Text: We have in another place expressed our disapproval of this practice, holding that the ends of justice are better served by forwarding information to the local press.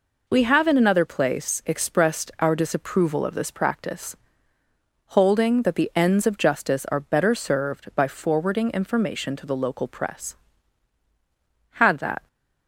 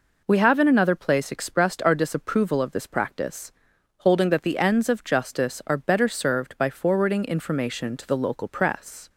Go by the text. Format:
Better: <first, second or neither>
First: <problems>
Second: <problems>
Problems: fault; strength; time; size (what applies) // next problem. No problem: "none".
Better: second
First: goes on to say "Had that"; from 11.7 s on; 0.52 s long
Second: none